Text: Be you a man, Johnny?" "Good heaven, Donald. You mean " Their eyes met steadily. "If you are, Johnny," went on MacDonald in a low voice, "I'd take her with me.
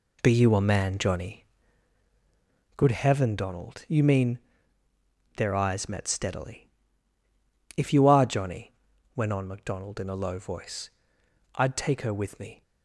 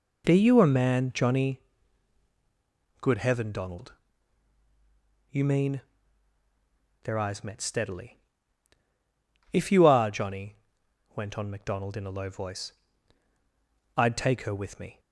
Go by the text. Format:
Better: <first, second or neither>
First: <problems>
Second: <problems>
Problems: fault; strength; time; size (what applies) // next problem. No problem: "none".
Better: neither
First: none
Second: none